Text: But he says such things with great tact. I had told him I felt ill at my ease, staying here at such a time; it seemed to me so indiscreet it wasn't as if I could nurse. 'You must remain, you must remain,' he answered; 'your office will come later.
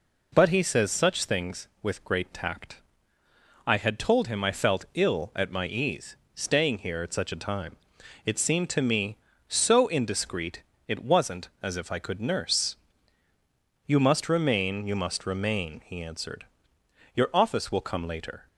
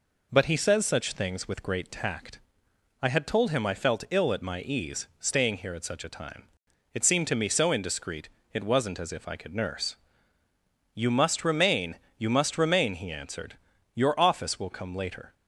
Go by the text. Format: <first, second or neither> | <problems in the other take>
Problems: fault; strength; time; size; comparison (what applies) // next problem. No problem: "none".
neither | pauses between "indiscreet" and "it"; slight; the same in both